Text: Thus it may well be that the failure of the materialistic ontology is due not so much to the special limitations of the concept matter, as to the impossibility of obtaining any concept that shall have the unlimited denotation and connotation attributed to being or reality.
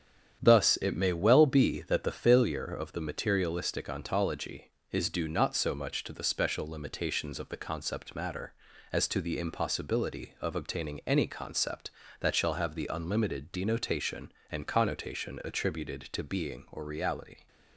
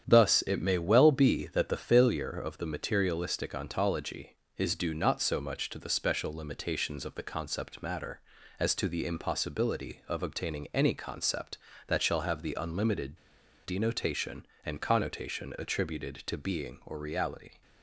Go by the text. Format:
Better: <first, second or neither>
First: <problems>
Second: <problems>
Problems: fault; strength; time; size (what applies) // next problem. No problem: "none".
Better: first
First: starts louder than the rest; strong; until 1.4 s; 9 dB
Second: starts louder than the rest; strong; until 1.0 s; 9 dB // pauses between "unlimited" and "denotation"; noticeable; at 13.1 s; 0.47 s long